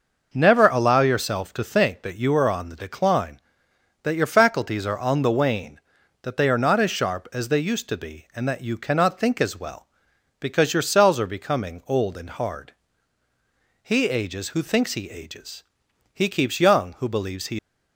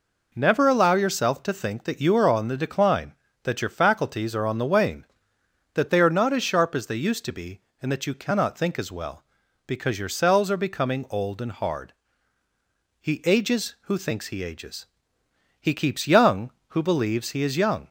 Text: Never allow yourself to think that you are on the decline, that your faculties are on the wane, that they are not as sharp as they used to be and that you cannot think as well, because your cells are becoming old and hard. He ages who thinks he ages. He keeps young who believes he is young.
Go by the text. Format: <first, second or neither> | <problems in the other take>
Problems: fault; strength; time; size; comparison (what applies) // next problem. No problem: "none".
second | stops before "is young"; at 17.5 s